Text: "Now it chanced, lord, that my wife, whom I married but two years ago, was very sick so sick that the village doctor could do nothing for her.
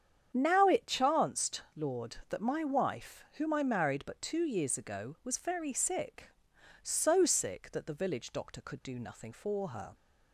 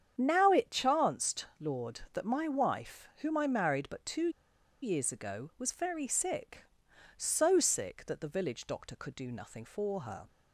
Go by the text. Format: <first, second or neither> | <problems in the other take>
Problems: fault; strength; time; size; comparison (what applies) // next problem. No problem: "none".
first | starts louder than the rest; strong; until 1.1 s; 8.5 dB; strong in the first // pauses between "two" and "years"; noticeable; at 4.2 s; 0.53 s long